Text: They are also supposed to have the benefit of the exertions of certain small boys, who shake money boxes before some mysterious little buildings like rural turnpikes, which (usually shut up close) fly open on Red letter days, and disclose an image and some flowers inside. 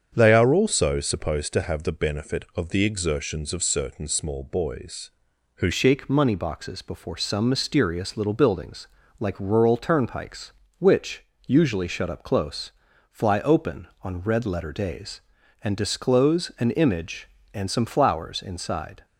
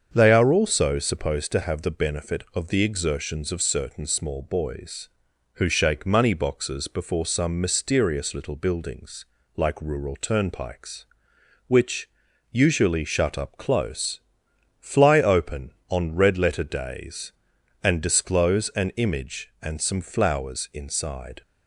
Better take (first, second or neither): second